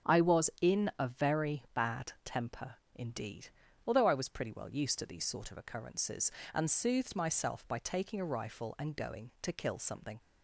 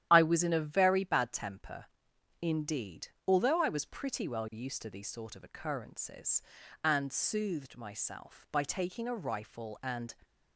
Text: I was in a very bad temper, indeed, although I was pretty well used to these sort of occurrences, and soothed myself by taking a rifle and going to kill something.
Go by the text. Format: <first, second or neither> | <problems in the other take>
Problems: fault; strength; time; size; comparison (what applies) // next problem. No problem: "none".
first | starts louder than the rest; strong; until 1.1 s; 11 dB; strong in the first // stops before "going to kill something"; at 10.2 s